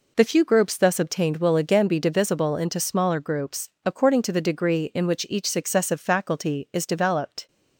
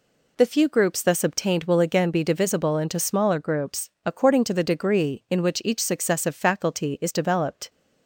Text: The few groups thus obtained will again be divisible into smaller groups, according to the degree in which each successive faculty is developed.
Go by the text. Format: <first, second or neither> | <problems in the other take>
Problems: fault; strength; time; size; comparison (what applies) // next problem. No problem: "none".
neither | none